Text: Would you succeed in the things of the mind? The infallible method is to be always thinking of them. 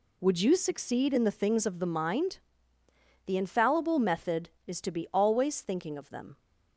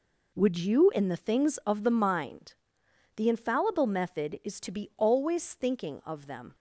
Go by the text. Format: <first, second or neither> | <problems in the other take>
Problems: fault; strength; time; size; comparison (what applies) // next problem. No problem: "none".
first | skips "succeed"; at 0.9 s